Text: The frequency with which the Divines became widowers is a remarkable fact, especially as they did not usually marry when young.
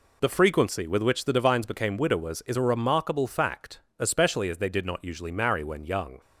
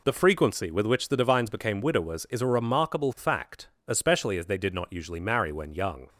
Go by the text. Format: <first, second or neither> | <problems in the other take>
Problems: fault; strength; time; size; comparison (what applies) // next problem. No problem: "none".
neither | none